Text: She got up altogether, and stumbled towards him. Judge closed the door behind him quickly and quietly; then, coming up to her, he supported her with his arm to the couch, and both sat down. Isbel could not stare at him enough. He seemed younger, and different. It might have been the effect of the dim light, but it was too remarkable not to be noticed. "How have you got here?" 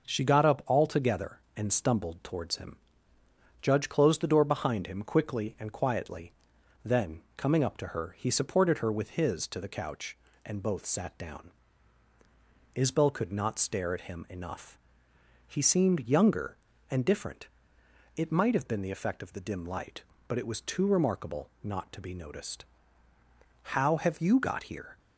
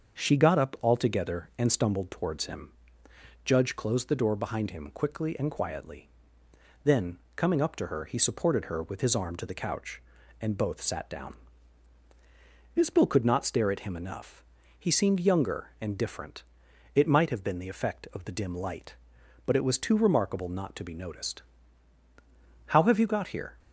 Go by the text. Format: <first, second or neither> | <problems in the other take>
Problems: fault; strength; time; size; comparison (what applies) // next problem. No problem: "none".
second | starts louder than the rest; noticeable; until 1.1 s; 6 dB; also in the second // skips "arm"; at 9.4 s